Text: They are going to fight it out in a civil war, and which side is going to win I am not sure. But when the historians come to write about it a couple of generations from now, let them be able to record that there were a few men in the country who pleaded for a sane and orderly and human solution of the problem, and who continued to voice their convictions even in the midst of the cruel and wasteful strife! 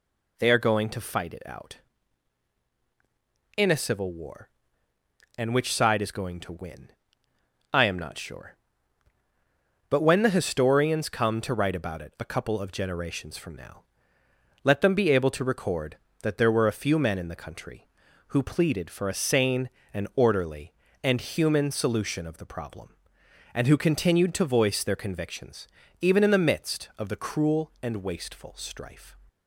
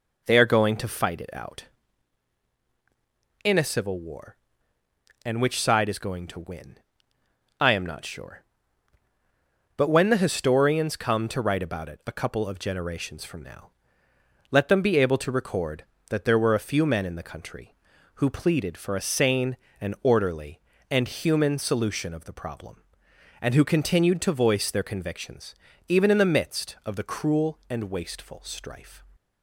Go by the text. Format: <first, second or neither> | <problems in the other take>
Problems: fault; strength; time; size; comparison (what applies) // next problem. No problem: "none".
first | starts louder than the rest; noticeable; until 2.0 s; 4.5 dB // pauses between "win" and "I"; noticeable; at 6.7 s; 0.82 s long; noticeable in the first // pauses between "convictions" and "even"; slight; at 25.5 s; 0.36 s long; slight in the first